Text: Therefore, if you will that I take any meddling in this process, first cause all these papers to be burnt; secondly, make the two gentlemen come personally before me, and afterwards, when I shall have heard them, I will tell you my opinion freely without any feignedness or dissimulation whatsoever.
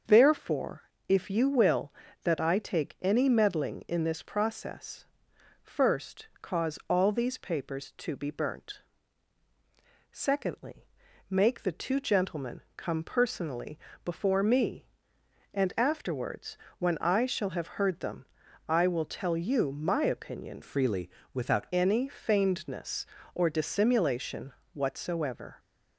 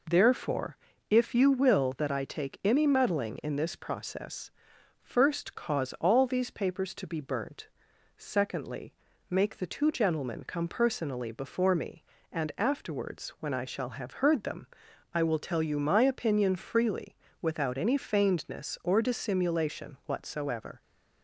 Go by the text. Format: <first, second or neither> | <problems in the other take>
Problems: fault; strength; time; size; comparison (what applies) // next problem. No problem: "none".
second | starts louder than the rest; until 1.3 s; 6.5 dB // pauses between "personally" and "before"; slight; at 13.7 s; 0.24 s long // changes voice from "freely" to "without"; from 20.6 to 21.6 s; 1.0 s long // pauses between "freely" and "without"; slight; at 21.0 s; 0.24 s long; slight in the second // pauses between "dissimulation" and "whatsoever"; slight; at 24.5 s; 0.22 s long